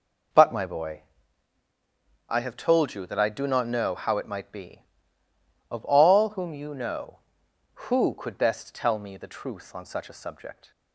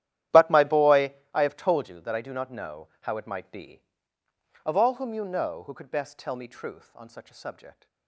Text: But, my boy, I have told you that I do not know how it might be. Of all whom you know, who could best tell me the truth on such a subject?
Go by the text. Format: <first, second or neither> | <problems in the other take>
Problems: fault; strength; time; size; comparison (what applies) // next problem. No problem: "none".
first | starts louder than the rest; strong; until 1.5 s; 12 dB // skips "the"; at 6.4 s